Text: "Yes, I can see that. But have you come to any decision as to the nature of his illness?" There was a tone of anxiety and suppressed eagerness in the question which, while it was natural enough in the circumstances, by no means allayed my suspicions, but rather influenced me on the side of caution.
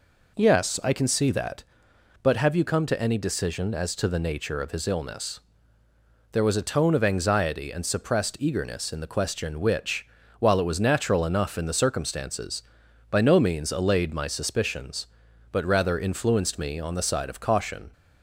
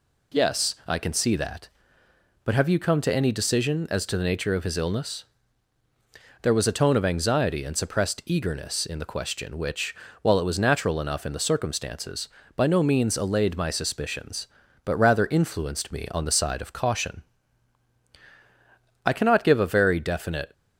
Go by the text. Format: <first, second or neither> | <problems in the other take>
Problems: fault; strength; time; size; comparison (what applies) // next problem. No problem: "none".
first | goes on to say "I cannot give a very definite"; from 19.0 s on; 1.4 s long